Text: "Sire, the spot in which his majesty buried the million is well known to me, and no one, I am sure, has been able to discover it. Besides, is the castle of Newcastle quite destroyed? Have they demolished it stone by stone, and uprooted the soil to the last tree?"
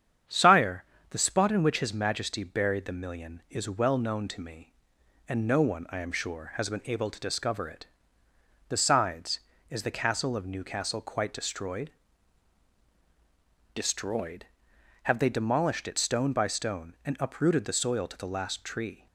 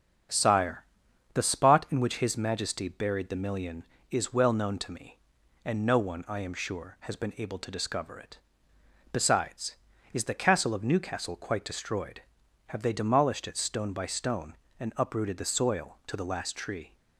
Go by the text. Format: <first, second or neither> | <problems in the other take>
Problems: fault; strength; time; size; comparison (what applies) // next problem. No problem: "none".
second | starts louder than the rest; strong; until 1.5 s; 8.5 dB; strong in the second // says "destroyed" twice; at 13.7 s